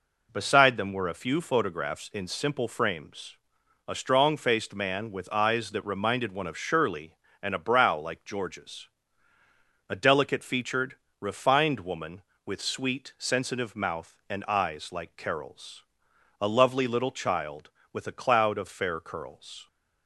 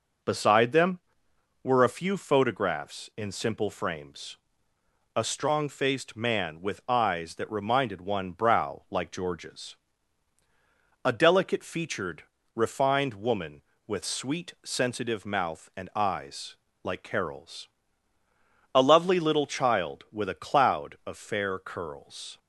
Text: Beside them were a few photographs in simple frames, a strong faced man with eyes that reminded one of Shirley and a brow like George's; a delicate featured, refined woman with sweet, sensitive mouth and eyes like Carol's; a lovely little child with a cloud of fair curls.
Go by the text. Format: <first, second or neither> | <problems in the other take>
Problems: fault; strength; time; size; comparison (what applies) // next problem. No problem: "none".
first | skips "of Shirley and a"; at 8.3 s // pauses between "eyes" and "like"; slight; at 16.5 s; 0.30 s long